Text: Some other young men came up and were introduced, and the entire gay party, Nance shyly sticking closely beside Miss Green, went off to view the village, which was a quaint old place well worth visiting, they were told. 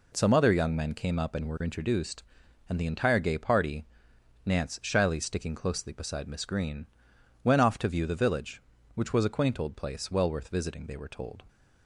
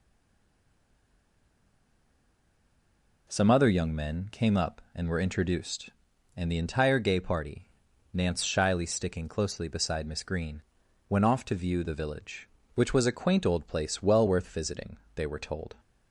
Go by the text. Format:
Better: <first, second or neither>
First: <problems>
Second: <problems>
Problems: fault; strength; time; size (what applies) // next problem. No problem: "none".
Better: first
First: none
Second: stays silent before the first word; strong; until 3.2 s; 3.2 s long